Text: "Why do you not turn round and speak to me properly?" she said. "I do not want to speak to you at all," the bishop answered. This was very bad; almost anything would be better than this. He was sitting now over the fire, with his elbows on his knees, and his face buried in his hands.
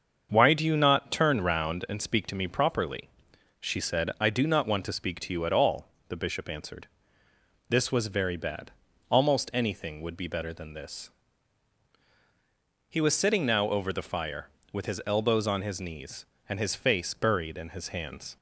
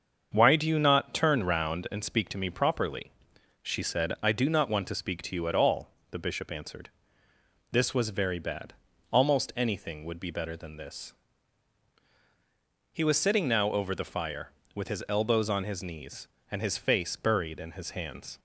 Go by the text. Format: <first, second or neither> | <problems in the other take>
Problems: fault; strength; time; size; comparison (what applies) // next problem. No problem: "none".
neither | starts louder than the rest; the same in both